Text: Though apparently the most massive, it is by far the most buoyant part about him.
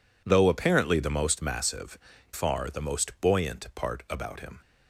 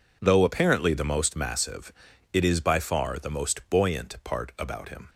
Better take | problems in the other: second | skips "it is by"; at 2.1 s

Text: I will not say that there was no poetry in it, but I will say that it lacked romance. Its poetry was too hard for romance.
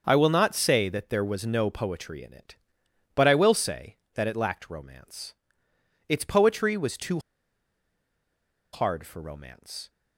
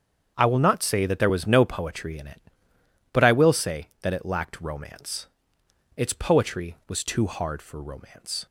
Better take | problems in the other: second | starts louder than the rest; until 1.0 s; 6.5 dB; strong in the second // pauses between "too" and "hard"; strong; at 7.2 s; 1.5 s long

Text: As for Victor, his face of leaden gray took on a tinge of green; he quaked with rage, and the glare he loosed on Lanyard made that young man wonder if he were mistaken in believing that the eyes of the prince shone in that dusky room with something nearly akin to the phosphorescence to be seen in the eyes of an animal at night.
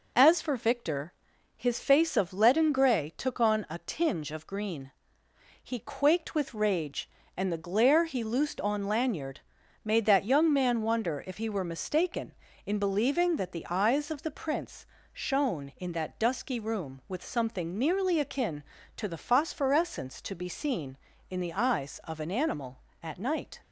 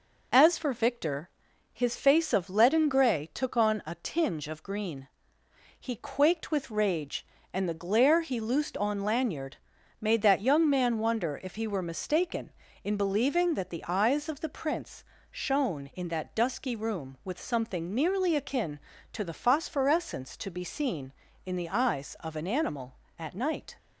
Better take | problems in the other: neither | pauses between "Lanyard" and "made"; noticeable; the same in both // pauses between "prince" and "shone"; slight; the same in both

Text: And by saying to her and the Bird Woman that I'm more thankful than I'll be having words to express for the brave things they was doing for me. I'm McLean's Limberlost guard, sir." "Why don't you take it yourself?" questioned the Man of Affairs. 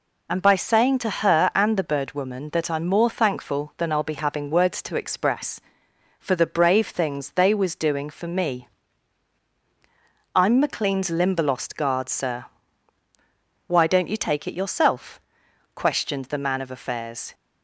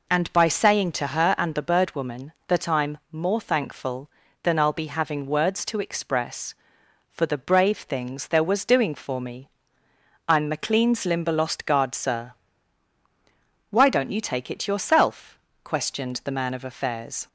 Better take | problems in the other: first | says "there" for "they"; at 8.2 s

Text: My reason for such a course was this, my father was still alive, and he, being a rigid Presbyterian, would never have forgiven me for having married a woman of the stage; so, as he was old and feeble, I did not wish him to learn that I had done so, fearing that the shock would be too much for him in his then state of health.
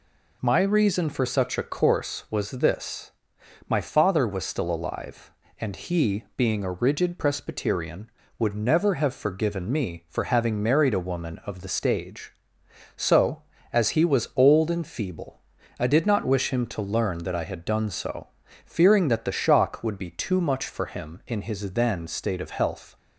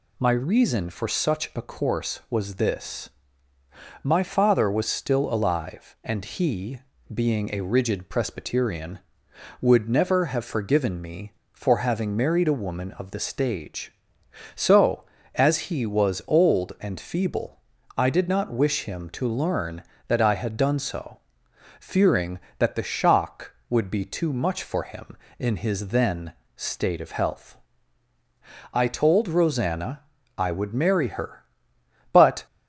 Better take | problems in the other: first | pauses between "then" and "state"; slight; at 26.3 s; 0.24 s long // goes on to say "I told Rosanna I would marry her but"; strong; from 28.7 s on; 3.7 s long

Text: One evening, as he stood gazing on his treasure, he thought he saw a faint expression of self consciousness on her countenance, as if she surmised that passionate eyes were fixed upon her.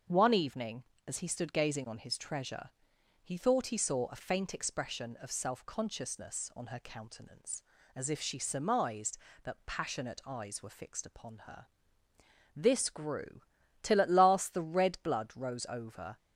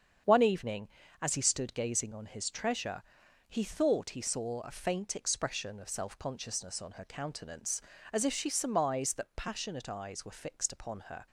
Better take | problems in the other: second | starts louder than the rest; until 1.3 s; 6.5 dB; strong in the second // goes on to say "This grew till at last the red blood rose over"; strong; from 12.5 s on; 3.6 s long

